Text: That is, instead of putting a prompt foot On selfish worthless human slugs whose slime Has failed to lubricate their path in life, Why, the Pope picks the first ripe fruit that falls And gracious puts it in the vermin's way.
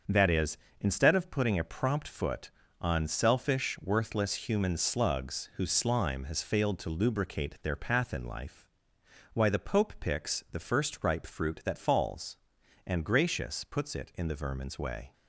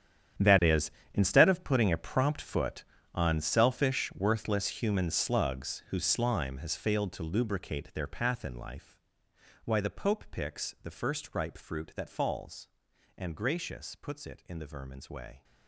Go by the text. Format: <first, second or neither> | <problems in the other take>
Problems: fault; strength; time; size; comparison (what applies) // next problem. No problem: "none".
first | gets quieter; strong; throughout; 15.5 dB // starts louder than the rest; strong; until 1.6 s; 9.5 dB; also in the first